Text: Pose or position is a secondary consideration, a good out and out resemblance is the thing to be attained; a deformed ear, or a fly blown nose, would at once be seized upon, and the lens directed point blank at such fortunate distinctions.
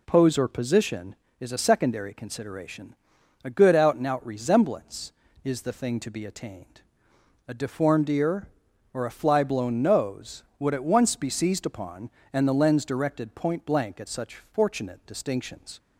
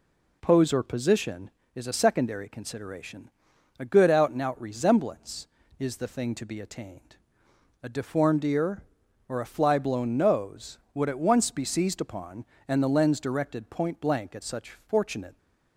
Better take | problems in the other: first | stops before "distinctions"; at 15.3 s

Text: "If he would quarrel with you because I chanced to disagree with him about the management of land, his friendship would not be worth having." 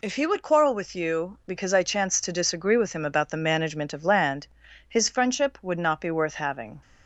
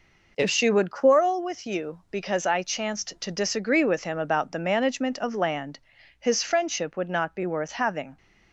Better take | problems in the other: first | says "she" for "he"; at 0.5 s

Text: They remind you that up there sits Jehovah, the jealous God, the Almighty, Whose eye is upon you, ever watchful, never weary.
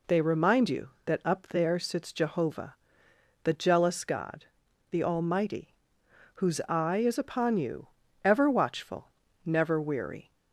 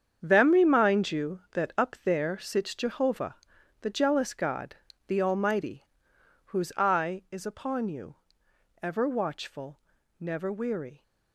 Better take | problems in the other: first | starts louder than the rest; strong; until 1.2 s; 7.5 dB // says "Them" for "They"; at 0.2 s

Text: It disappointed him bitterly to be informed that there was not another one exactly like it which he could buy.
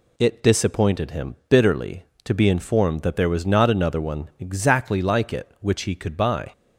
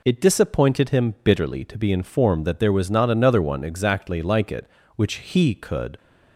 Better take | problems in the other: first | stops before "buy"; at 5.9 s

